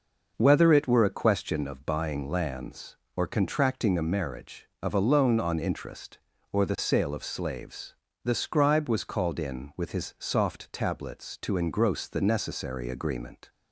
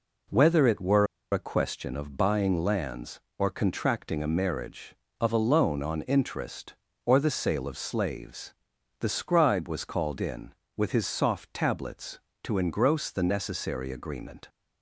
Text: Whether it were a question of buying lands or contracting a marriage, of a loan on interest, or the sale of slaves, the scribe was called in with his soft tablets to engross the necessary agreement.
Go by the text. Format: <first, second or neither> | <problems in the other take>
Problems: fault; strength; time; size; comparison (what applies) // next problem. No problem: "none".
first | pauses between "were" and "a"; slight; at 1.0 s; 0.26 s long